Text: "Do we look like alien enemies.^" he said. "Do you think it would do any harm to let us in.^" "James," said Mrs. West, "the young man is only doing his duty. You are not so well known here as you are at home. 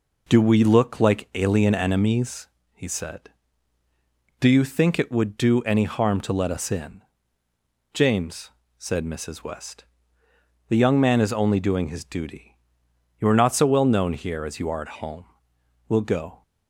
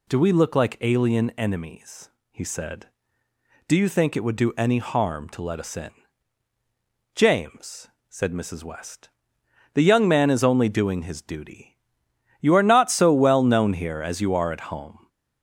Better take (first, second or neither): second